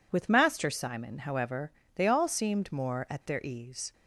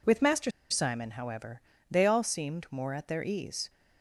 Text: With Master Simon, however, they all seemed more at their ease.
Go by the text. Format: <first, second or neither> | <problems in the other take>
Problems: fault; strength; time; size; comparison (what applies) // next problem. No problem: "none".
first | pauses between "Master" and "Simon"; slight; at 0.5 s; 0.20 s long